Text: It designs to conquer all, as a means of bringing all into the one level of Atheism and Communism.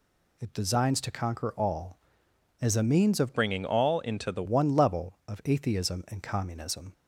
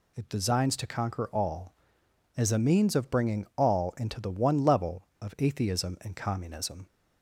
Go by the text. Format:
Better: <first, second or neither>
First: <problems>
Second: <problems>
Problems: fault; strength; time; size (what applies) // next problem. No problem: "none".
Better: second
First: changes voice from "bringing" to "the"; from 3.3 to 4.4 s; 1.1 s long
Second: none